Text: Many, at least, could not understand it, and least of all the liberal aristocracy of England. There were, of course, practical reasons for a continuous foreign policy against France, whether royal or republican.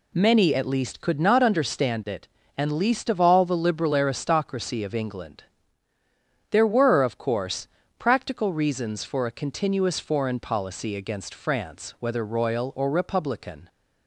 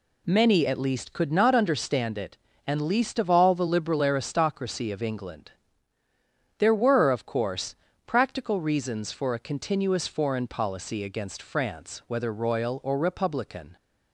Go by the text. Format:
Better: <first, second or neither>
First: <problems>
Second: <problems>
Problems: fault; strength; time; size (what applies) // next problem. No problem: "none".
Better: neither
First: none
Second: none